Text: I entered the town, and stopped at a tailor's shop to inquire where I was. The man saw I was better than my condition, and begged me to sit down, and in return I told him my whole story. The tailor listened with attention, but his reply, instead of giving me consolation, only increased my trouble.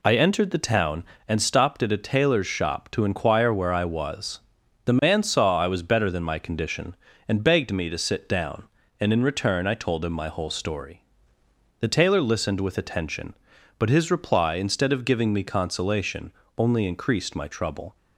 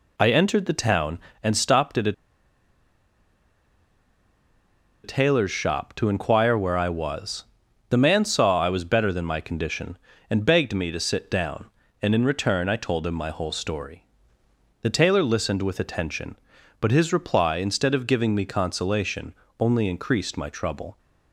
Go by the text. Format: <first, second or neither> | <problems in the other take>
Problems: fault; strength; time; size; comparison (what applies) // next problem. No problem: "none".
first | pauses between "a" and "tailor's"; strong; at 2.1 s; 2.9 s long